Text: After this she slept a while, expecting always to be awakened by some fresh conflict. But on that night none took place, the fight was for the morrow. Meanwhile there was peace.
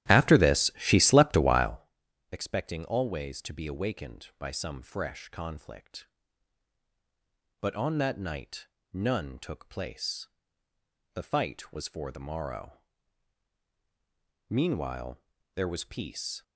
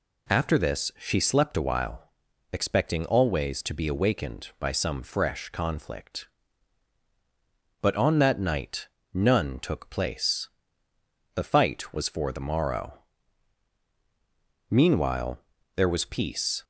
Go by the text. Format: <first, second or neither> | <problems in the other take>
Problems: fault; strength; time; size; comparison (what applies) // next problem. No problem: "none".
second | starts louder than the rest; strong; until 1.9 s; 13.5 dB // pauses between "night" and "none"; slight; at 8.6 s; 0.26 s long; slight in the second // pauses between "Meanwhile" and "there"; slight; at 15.1 s; 0.36 s long; slight in the second